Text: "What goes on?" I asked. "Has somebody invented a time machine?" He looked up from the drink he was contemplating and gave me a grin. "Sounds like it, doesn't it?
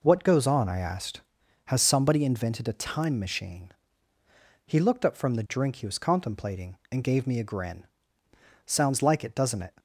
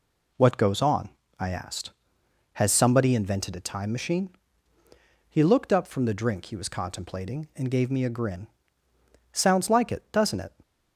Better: neither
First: none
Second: none

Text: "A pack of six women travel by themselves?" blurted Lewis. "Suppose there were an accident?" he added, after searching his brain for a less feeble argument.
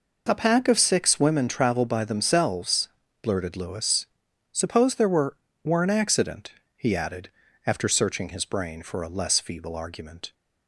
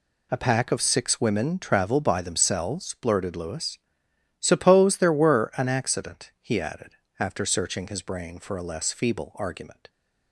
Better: second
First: says "were" twice; at 5.6 s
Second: none

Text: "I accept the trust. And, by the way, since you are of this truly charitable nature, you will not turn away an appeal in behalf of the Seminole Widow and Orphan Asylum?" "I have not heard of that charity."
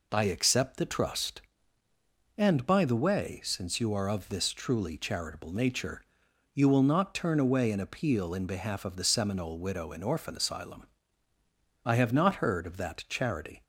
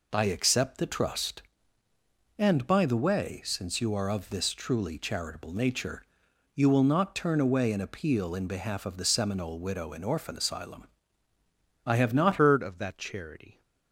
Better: first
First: none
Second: changes voice at "heard"; from 12.3 s on; 1.3 s long

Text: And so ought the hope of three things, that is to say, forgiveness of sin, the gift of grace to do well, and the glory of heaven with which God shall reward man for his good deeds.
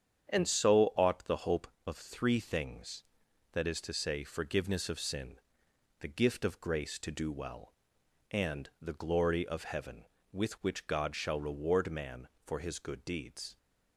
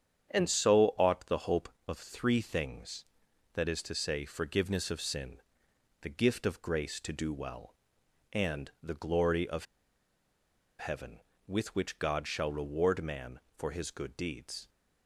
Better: first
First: starts louder than the rest; strong; until 1.3 s; 8.5 dB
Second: starts louder than the rest; strong; until 1.3 s; 8.5 dB // pauses between "of" and "heaven"; at 9.6 s; 1.1 s long

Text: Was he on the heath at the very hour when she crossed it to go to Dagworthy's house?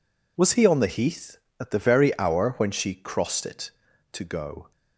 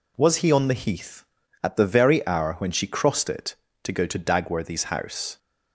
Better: second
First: stops before "to Dagworthy's house"; at 4.7 s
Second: none

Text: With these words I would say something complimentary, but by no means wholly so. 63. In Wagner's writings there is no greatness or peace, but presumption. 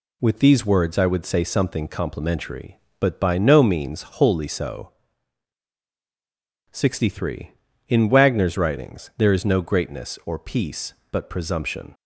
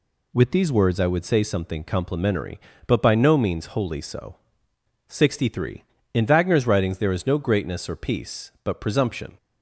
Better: neither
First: none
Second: none

